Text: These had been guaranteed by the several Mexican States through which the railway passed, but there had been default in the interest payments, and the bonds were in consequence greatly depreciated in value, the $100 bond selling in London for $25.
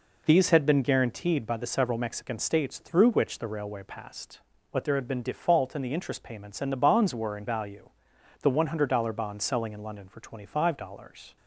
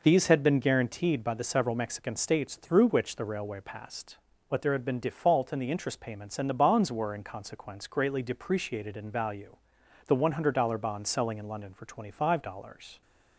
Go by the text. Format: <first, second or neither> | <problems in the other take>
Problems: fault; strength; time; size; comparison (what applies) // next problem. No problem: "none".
second | skips "consequence greatly depreciated in"; at 7.4 s